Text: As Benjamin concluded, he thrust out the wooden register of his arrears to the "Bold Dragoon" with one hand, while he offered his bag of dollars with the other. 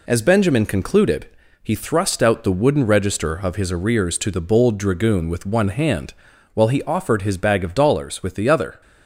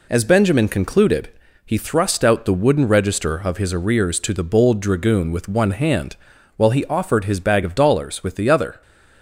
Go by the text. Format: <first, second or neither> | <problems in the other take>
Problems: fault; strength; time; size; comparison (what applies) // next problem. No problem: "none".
neither | none